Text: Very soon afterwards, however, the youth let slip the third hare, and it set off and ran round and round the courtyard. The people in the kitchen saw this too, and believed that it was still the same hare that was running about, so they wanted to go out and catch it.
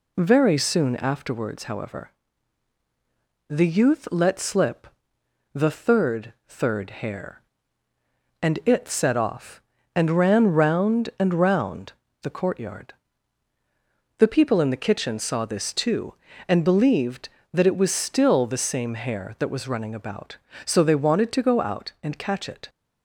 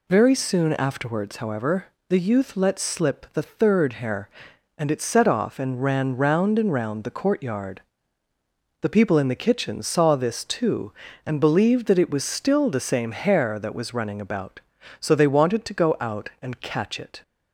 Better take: second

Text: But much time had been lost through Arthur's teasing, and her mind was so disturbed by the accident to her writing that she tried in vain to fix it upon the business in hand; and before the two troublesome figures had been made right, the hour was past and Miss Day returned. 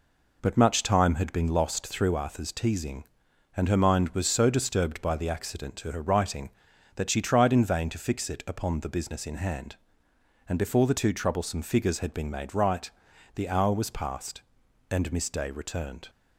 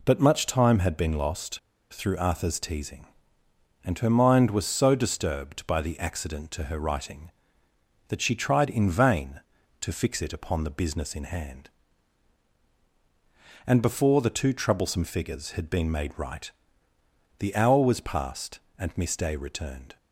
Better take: first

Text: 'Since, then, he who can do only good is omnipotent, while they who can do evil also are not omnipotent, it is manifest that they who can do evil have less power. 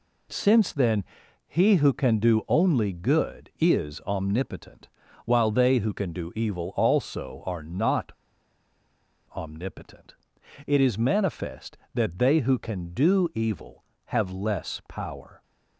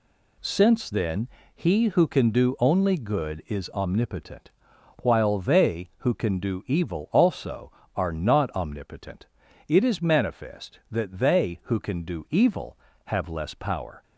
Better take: second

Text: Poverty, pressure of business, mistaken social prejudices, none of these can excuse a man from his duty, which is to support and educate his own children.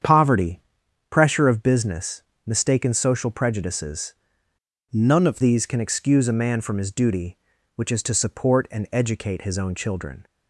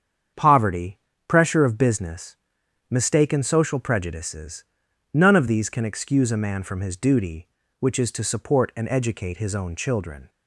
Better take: second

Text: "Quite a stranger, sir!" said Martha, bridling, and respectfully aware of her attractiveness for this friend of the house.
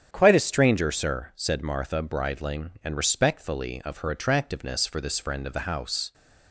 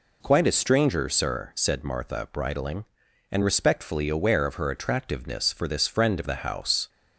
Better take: second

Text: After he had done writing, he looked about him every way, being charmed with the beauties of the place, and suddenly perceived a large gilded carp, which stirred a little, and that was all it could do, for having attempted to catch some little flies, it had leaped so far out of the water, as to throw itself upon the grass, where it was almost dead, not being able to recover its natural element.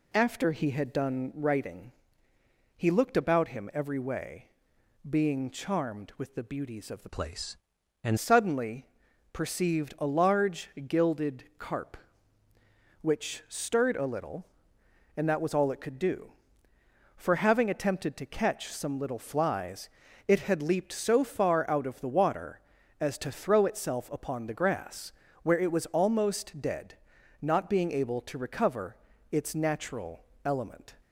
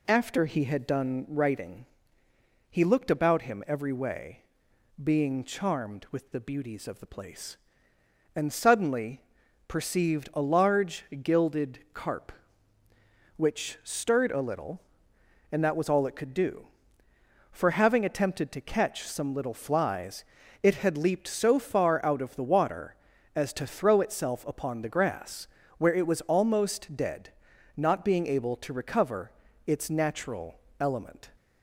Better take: second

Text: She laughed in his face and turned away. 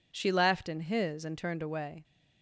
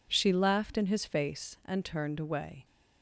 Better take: second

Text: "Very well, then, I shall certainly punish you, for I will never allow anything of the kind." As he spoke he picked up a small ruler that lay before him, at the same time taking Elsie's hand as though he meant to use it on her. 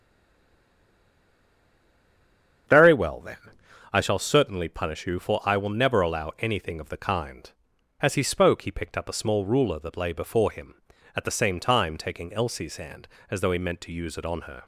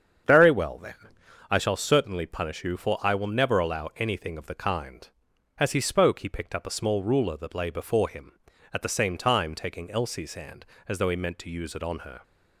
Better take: second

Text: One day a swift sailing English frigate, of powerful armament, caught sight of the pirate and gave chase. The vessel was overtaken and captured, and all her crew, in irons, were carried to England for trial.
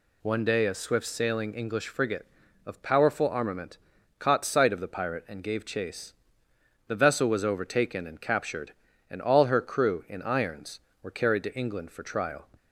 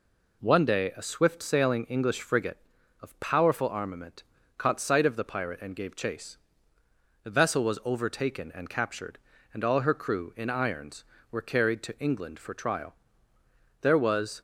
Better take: first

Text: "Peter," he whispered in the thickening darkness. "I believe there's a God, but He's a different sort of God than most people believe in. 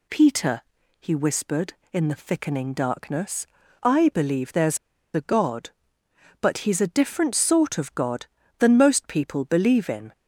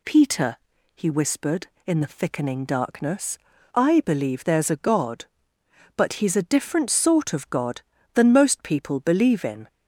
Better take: second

